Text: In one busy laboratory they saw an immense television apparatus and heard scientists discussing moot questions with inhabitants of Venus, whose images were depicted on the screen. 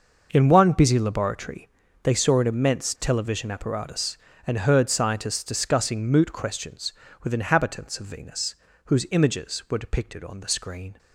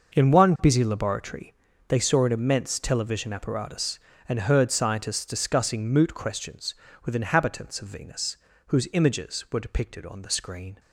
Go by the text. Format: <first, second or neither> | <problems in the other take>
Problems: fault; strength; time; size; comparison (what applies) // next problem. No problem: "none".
neither | pauses between "laboratory" and "they"; slight; the same in both